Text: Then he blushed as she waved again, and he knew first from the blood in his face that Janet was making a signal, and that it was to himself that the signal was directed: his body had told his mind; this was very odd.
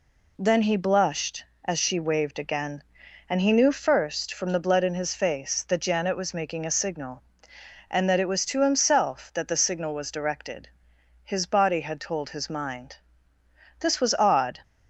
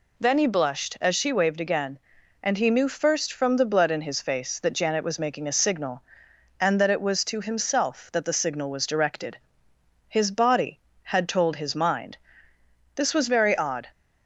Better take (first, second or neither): second